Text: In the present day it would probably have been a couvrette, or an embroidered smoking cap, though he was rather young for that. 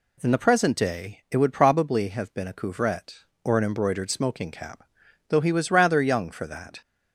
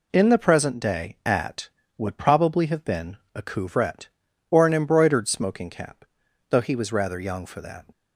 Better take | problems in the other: first | says "at" for "it"; at 1.2 s // pauses between "been" and "a"; slight; at 3.1 s; 0.18 s long

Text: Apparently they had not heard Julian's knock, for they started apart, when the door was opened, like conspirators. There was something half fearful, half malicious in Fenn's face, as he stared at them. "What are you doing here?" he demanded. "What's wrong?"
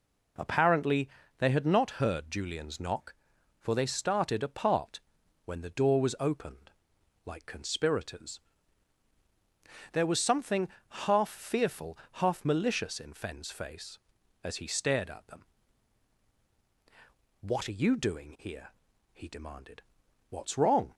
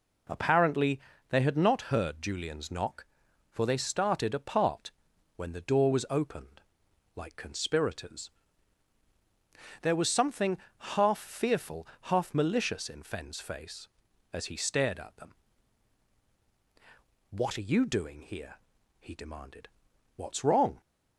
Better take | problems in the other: neither | pauses between "Apparently" and "they"; slight; the same in both // pauses between "something" and "half"; slight; the same in both

